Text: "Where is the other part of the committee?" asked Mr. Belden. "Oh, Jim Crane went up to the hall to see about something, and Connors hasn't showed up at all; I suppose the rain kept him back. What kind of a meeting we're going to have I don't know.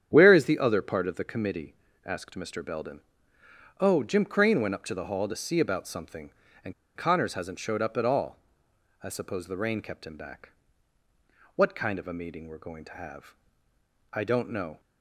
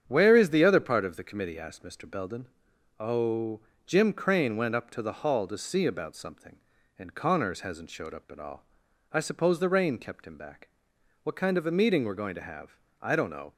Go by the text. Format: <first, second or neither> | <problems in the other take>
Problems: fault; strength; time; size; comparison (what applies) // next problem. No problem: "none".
second | starts louder than the rest; strong; until 1.1 s; 9 dB; strong in the second // pauses between "and" and "Connors"; slight; at 6.7 s; 0.24 s long // pauses between "have" and "I"; noticeable; at 13.3 s; 0.76 s long; slight in the second